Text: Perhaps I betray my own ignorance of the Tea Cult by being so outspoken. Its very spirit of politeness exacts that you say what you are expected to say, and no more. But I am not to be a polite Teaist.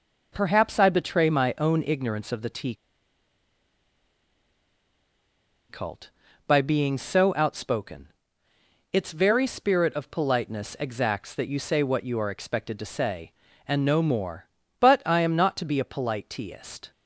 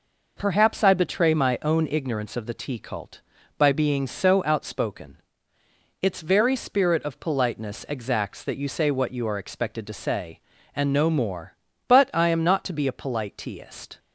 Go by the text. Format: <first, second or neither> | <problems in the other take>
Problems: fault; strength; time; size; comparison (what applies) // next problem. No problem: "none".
second | pauses between "Tea" and "Cult"; strong; at 2.7 s; 2.9 s long